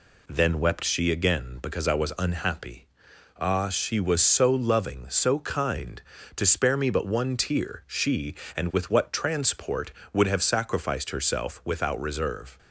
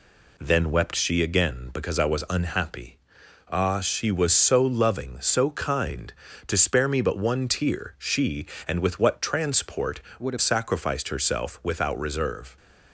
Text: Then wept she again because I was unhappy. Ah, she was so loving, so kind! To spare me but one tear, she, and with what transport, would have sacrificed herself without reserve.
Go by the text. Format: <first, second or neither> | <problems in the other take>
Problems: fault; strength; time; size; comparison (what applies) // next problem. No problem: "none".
first | changes voice from "would" to "have"; from 10.2 to 10.3 s; 0.1 s long